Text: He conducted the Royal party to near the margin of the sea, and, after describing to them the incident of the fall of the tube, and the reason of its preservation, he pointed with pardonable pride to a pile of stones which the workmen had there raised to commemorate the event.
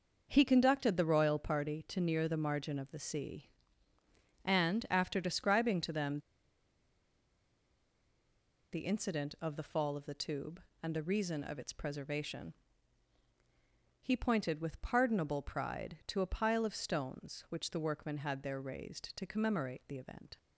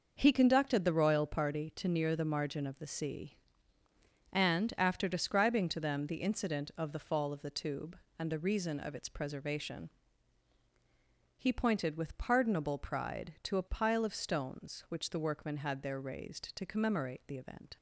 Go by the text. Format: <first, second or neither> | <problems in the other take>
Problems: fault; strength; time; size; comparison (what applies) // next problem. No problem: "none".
second | pauses between "them" and "the"; strong; at 6.1 s; 2.5 s long